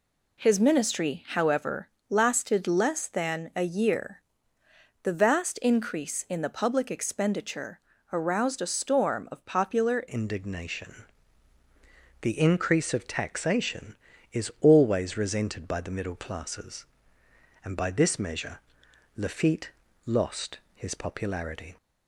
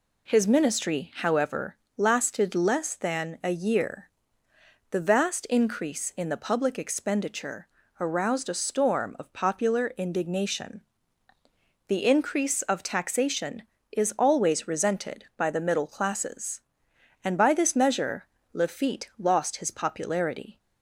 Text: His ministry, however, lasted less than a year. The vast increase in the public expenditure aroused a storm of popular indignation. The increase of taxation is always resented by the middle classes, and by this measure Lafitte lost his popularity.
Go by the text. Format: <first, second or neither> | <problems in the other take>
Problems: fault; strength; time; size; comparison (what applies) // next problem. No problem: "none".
second | pauses between "expenditure" and "aroused"; slight; at 7.8 s; 0.32 s long; slight in the second // changes voice at "indignation"; from 10.0 s on; 11.7 s long // pauses between "measure" and "Lafitte"; noticeable; at 18.5 s; 0.58 s long; slight in the second // pauses between "Lafitte" and "lost"; slight; at 19.7 s; 0.34 s long // pauses between "lost" and "his"; slight; at 20.5 s; 0.16 s long